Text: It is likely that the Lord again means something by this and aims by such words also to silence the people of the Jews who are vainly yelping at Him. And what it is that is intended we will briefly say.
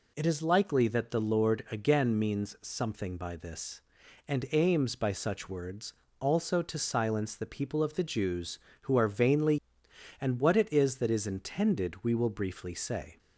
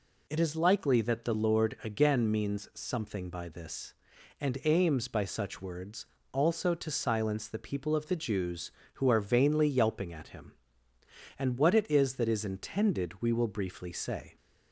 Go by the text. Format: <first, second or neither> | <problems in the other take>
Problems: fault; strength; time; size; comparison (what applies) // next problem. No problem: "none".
second | pauses between "words" and "also"; slight; at 5.9 s; 0.26 s long; slight in the second // skips "yelping at Him"; at 9.8 s